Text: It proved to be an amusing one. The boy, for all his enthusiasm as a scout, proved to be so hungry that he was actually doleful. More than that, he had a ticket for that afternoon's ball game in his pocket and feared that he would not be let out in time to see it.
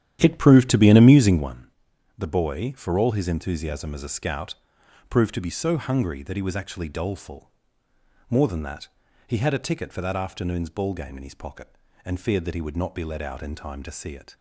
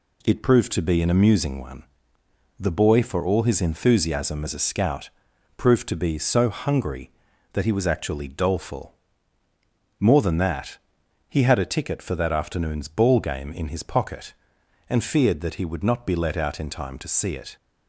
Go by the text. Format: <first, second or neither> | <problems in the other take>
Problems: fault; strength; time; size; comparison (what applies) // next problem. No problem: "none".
second | starts louder than the rest; strong; until 1.5 s; 11 dB